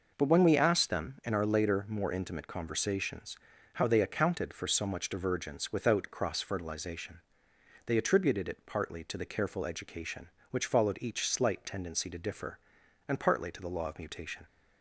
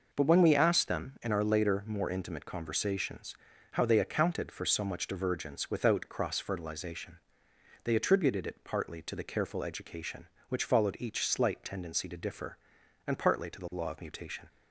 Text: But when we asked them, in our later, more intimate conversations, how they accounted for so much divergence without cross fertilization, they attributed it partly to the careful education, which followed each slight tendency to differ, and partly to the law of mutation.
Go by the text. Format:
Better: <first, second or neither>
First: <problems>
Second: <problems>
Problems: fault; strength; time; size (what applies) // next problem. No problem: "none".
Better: neither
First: none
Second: none